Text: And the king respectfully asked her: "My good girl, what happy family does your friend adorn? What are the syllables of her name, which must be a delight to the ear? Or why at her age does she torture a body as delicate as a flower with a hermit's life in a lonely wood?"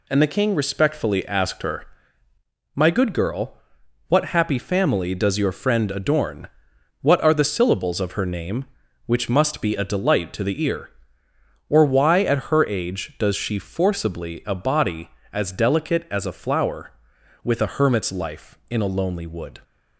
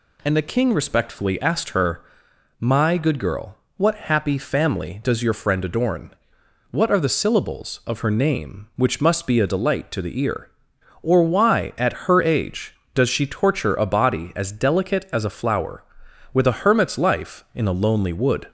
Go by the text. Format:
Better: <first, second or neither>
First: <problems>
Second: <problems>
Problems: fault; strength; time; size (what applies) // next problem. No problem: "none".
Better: second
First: says "forcibly" for "torture"; at 13.5 s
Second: none